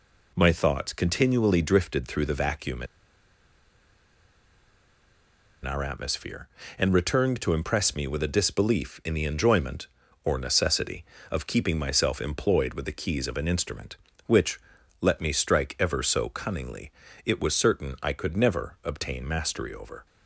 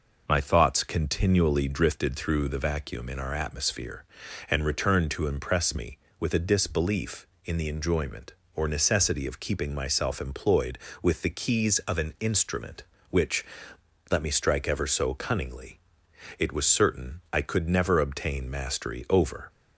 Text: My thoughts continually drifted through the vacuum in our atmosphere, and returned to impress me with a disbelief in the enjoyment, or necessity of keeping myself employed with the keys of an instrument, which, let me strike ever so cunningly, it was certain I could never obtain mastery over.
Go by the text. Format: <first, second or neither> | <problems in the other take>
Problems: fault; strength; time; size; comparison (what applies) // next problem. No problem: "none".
second | pauses between "in" and "our"; strong; at 2.8 s; 2.7 s long